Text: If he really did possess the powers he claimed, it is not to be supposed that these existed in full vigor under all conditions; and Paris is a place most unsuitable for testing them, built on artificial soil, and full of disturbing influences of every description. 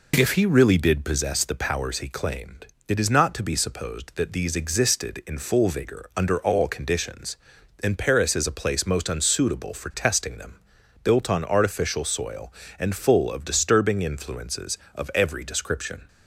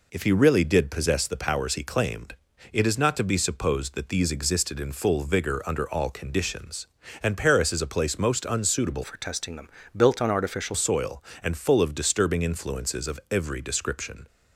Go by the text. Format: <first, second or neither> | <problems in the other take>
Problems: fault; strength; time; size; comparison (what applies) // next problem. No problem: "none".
first | changes voice from "for" to "artificial"; from 9.0 to 10.7 s; 1.7 s long